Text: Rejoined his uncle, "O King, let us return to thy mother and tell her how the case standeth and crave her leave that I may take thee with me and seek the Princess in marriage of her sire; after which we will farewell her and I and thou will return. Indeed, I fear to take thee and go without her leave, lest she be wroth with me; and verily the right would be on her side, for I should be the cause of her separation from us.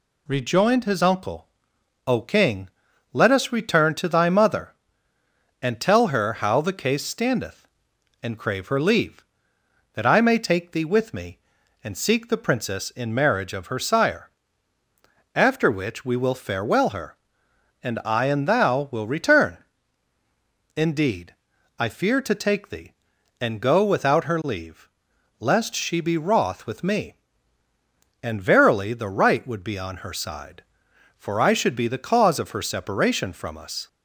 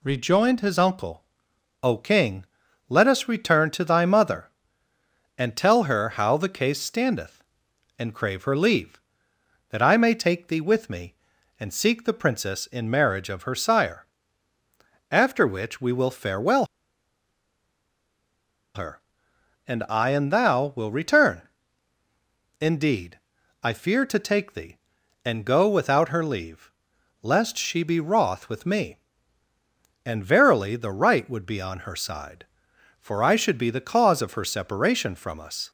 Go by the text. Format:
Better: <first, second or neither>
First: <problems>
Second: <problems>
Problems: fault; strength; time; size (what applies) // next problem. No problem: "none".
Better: first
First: none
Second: pauses between "farewell" and "her"; strong; at 16.6 s; 2.0 s long